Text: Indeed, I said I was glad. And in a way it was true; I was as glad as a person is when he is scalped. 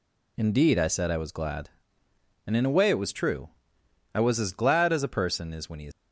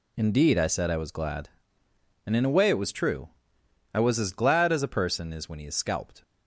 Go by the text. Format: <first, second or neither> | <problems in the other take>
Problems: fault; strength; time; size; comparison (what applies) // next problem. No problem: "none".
second | stops before "scalped"; at 5.9 s